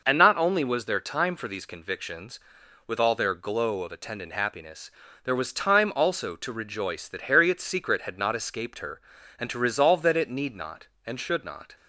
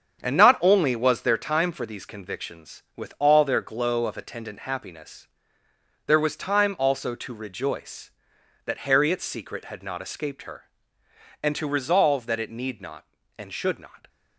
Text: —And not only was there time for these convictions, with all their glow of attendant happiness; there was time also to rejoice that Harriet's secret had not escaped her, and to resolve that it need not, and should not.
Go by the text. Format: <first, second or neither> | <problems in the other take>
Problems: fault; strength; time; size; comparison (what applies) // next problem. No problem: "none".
first | gets quieter; strong; throughout; 7 dB